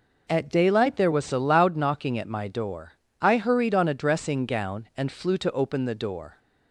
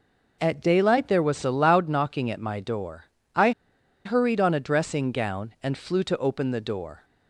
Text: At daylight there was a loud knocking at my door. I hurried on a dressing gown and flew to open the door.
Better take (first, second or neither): first